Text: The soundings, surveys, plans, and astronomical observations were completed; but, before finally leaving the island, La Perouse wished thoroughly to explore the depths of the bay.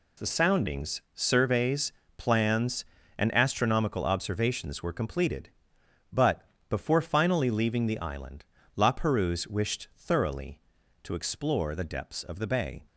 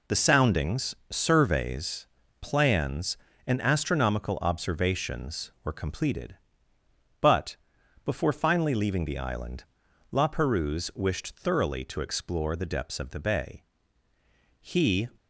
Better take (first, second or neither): first